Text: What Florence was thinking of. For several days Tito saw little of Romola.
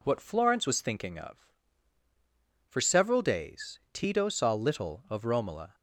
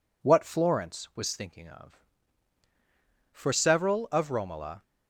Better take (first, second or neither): first